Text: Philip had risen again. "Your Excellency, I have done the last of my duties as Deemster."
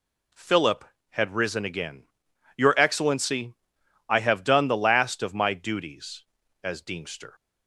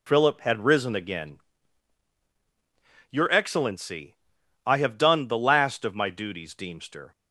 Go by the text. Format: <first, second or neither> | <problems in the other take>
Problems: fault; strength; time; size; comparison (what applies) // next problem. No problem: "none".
first | skips "as"; at 6.5 s